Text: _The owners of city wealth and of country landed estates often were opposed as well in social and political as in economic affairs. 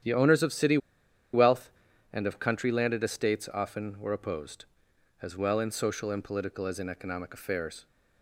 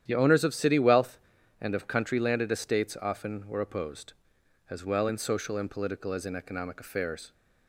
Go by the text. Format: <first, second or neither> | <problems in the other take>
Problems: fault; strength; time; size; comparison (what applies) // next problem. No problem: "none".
second | starts louder than the rest; strong; until 1.6 s; 10 dB; strong in the second // pauses between "city" and "wealth"; noticeable; at 0.7 s; 0.56 s long